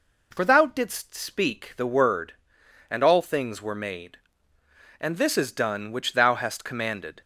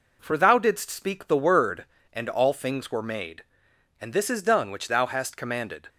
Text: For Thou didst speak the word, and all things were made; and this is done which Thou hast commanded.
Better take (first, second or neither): neither